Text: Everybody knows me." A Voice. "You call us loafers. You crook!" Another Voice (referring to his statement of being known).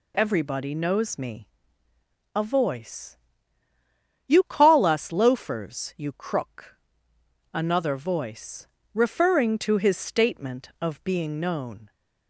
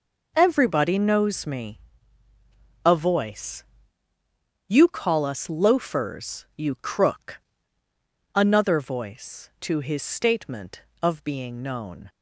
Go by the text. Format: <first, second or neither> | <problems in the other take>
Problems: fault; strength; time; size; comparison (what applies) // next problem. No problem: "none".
first | skips "referring"; at 9.5 s